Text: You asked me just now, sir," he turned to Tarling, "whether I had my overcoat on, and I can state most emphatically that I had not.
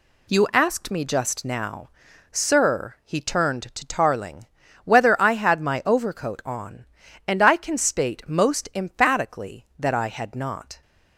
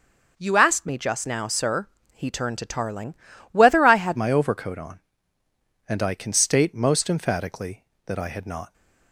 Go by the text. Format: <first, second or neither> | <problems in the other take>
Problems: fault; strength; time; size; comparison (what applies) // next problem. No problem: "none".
first | changes voice at "my"; from 4.1 s on; 4.6 s long